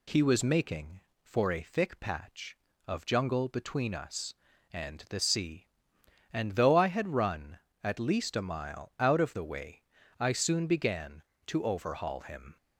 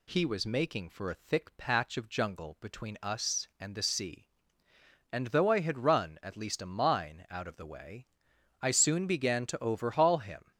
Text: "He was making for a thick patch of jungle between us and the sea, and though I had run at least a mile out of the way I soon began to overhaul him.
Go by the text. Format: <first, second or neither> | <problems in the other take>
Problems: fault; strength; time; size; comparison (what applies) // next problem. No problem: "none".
first | says "mine" for "mile"; at 6.6 s // pauses between "way" and "I"; noticeable; at 8.0 s; 0.52 s long; slight in the first